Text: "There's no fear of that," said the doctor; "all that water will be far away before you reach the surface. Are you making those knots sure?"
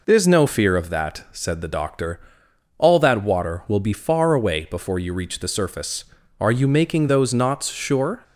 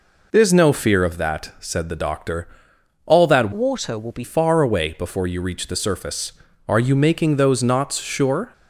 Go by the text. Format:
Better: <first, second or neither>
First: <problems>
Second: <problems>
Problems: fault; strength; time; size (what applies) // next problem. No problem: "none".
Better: first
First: none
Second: changes voice from "water" to "be"; from 3.5 to 4.2 s; 0.7 s long